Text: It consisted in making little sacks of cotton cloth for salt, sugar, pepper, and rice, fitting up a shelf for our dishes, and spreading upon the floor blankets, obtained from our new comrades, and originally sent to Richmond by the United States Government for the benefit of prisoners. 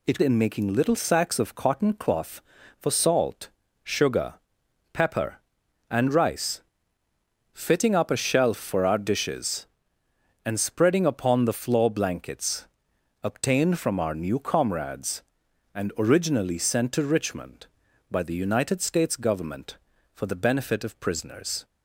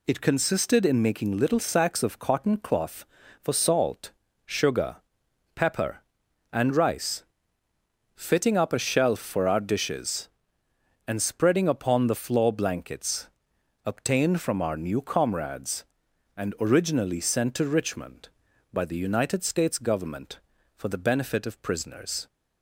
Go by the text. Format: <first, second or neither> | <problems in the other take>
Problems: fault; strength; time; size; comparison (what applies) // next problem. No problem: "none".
second | skips "consisted"; at 0.2 s